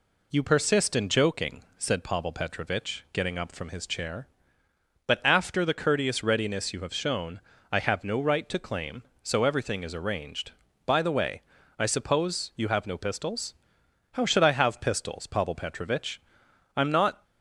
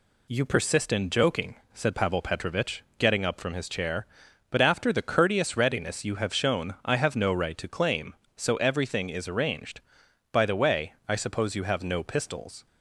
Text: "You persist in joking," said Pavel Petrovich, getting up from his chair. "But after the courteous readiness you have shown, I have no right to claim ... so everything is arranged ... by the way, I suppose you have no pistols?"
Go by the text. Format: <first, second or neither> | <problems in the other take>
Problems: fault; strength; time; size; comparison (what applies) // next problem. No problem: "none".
second | goes on to say "How should I have pistols Pavel Petrovich I'm not"; strong; from 14.1 s on; 3.1 s long